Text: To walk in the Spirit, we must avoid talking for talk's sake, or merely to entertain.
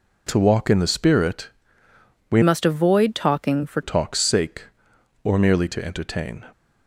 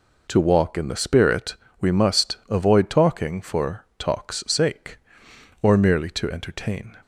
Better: second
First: changes voice from "must" to "for"; from 2.4 to 3.8 s; 1.4 s long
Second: none

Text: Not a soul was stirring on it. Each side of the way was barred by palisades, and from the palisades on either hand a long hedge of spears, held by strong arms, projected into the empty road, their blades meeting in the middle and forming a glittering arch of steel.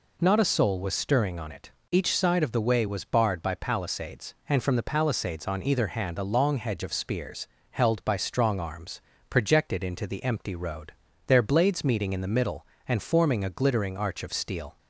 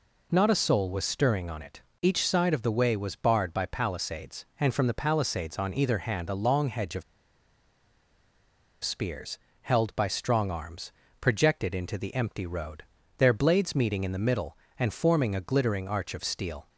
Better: first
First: none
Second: pauses between "of" and "spears"; strong; at 7.0 s; 1.8 s long

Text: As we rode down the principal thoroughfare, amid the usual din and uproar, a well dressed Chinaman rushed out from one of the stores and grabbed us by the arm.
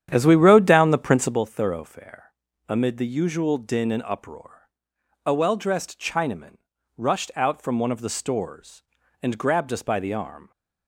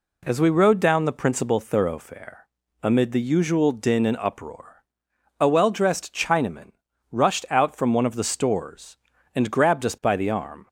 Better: second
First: starts louder than the rest; strong; until 1.5 s; 10 dB // pauses between "Chinaman" and "rushed"; at 6.5 s; 0.42 s long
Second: pauses between "Chinaman" and "rushed"; at 6.6 s; 0.42 s long

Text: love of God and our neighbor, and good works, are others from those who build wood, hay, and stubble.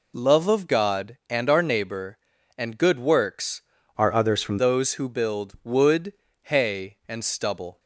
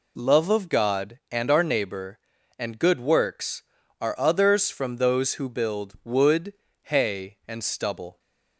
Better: second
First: changes voice from "are" to "from"; from 3.9 to 4.5 s; 0.6 s long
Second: none

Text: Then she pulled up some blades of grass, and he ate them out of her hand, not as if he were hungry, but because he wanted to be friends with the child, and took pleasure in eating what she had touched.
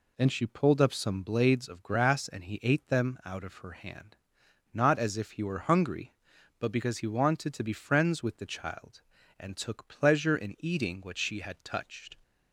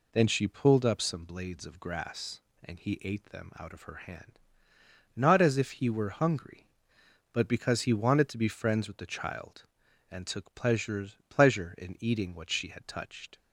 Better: first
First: none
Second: says "pleasure" twice; at 11.2 s

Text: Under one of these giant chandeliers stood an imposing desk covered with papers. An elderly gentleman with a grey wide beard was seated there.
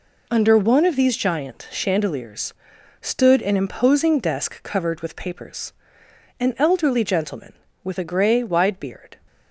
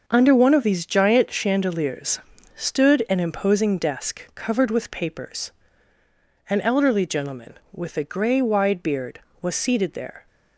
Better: second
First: pauses between "chandeliers" and "stood"; noticeable; at 2.5 s; 0.48 s long // stops before "was seated there"; at 9.2 s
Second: pauses between "chandeliers" and "stood"; slight; at 2.2 s; 0.34 s long

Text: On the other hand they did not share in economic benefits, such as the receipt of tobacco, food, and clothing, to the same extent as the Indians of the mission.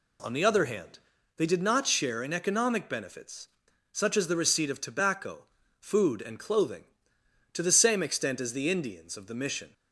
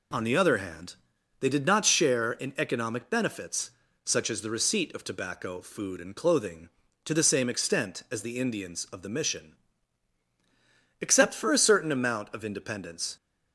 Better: first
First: pauses between "hand" and "they"; at 0.9 s; 0.38 s long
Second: pauses between "hand" and "they"; at 0.9 s; 0.44 s long // goes on to say "Except for a certain amount of independence"; strong; from 11.0 s on; 2.1 s long

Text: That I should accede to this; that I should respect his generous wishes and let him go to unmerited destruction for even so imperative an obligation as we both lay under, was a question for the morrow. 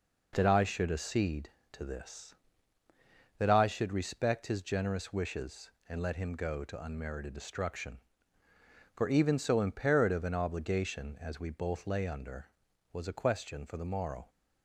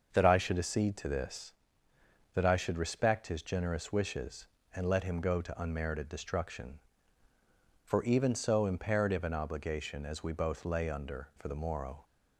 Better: first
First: none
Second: starts louder than the rest; until 1.1 s; 6 dB // skips "was a question"; at 11.3 s

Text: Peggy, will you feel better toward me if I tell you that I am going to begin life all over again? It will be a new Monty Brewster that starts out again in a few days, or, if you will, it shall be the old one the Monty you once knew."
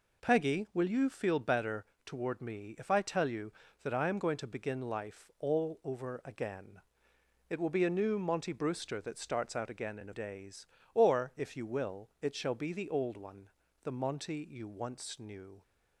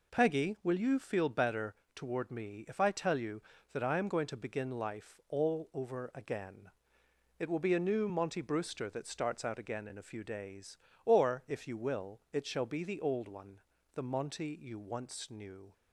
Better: second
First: pauses between "better" and "toward"; slight; at 1.8 s; 0.18 s long // skips "few"; at 10.1 s // pauses between "one" and "the"; slight; at 13.4 s; 0.34 s long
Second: pauses between "better" and "toward"; slight; at 1.7 s; 0.18 s long // pauses between "one" and "the"; slight; at 13.6 s; 0.34 s long

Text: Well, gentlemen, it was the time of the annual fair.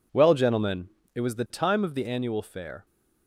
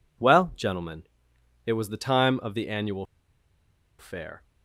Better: first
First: none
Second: pauses between "annual" and "fair"; noticeable; at 3.0 s; 0.93 s long

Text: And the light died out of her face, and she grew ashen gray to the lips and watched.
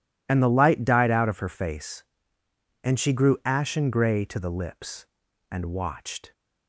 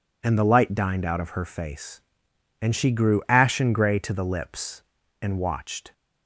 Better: first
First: none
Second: says "dined" for "died"; at 0.7 s

